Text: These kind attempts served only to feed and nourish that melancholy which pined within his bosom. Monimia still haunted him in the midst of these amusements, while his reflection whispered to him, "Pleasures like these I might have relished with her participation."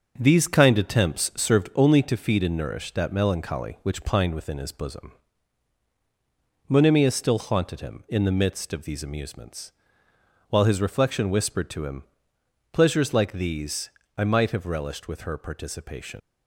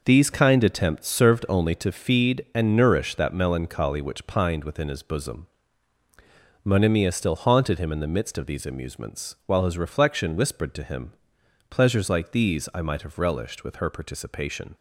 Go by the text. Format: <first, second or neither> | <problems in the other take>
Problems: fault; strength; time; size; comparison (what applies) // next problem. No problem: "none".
second | starts louder than the rest; until 1.1 s; 6.5 dB // pauses between "these" and "I"; slight; at 13.9 s; 0.26 s long // leaves "participation" unfinished; at 16.1 s; 85 ms